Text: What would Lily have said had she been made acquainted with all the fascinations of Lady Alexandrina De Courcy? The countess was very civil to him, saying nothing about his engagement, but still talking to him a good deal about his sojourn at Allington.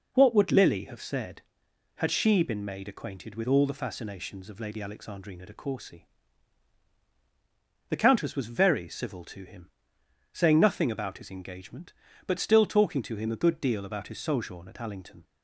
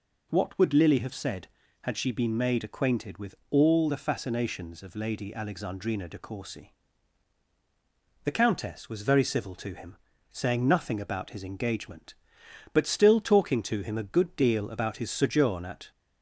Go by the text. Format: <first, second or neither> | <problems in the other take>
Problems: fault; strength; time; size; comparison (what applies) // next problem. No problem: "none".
first | pauses between "with" and "all"; slight; at 3.3 s; 0.16 s long // stops before "Allington"; at 15.9 s